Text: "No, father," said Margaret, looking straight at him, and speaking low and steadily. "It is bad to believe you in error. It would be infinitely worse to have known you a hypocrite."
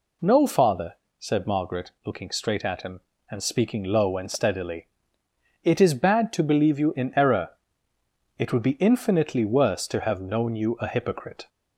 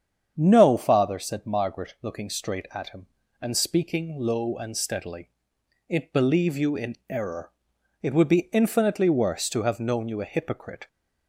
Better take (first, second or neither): first